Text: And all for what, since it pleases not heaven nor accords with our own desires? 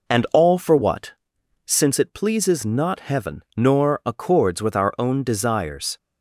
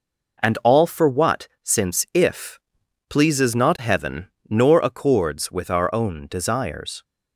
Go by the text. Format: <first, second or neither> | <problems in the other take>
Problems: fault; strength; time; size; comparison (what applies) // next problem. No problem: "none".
first | says "if" for "it"; at 2.1 s // pauses between "heaven" and "nor"; slight; at 4.2 s; 0.20 s long